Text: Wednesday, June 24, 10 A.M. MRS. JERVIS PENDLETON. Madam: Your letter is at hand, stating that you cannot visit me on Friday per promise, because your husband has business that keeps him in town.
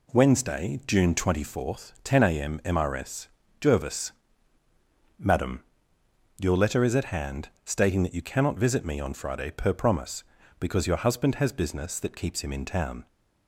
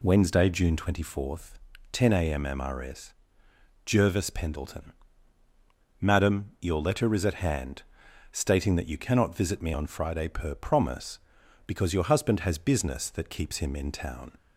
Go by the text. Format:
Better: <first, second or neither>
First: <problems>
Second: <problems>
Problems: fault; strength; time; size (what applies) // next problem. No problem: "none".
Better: second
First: skips "PENDLETON"; at 4.6 s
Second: none